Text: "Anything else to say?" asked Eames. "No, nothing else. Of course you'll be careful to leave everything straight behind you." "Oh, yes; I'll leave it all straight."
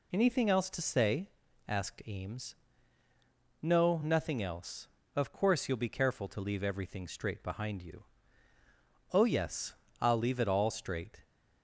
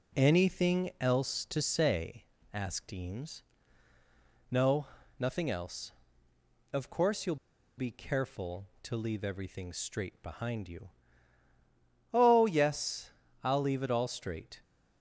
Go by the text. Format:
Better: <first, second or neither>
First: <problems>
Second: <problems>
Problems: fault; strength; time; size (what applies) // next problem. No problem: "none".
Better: first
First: none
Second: pauses between "you'll" and "be"; at 7.3 s; 0.42 s long